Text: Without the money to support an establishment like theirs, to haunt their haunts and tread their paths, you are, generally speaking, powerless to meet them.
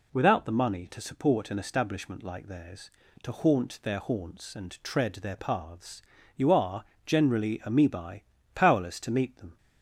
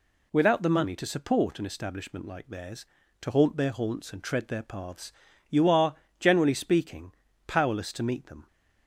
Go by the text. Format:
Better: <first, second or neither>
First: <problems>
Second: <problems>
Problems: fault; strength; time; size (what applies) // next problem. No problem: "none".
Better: second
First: says "amoebae" for "speaking"; at 7.6 s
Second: none